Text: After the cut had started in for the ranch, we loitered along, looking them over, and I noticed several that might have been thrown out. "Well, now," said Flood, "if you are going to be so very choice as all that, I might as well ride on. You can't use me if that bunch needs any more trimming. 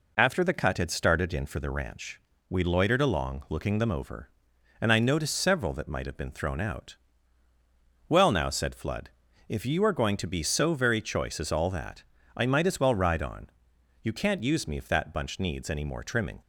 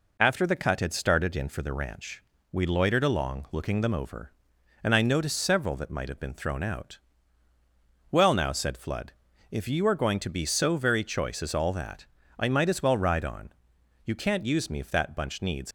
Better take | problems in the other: first | stops before "any more trimming"; at 15.6 s

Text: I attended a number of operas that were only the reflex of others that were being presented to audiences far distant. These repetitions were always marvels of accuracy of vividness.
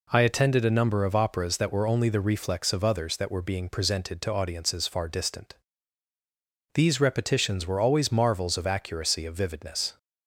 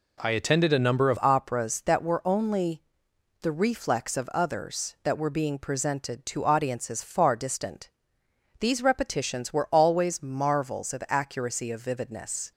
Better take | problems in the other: first | changes voice at "operas"; from 1.2 s on; 11.3 s long // pauses between "only" and "the"; noticeable; at 2.8 s; 0.58 s long

